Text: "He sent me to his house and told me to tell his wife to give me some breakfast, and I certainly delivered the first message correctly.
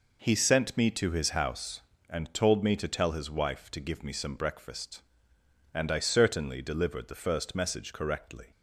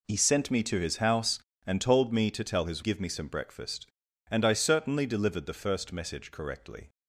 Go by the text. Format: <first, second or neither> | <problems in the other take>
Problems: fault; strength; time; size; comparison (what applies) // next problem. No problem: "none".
first | skips "wife to"; at 2.8 s